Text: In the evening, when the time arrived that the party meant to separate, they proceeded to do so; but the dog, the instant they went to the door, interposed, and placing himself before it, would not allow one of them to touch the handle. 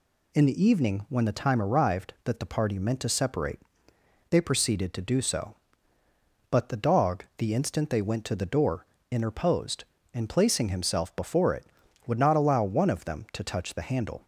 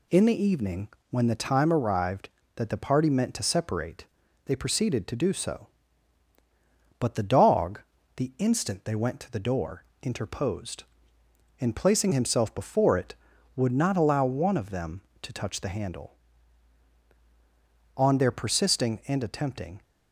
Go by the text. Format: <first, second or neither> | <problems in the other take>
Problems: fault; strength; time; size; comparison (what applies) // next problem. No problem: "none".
first | goes on to say "On their persisting and attempting"; strong; from 17.9 s on; 1.8 s long